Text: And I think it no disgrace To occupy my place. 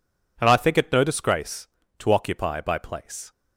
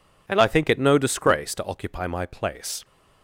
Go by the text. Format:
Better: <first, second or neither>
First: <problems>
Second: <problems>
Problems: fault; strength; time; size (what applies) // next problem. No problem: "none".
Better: second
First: says "by" for "my"; at 2.6 s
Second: none